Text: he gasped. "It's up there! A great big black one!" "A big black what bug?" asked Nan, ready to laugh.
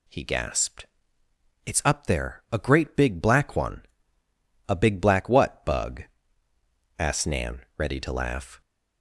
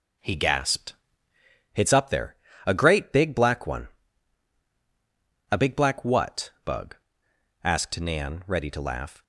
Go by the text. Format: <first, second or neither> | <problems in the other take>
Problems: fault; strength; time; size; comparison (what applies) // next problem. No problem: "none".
first | starts louder than the rest; noticeable; until 1.6 s; 5.5 dB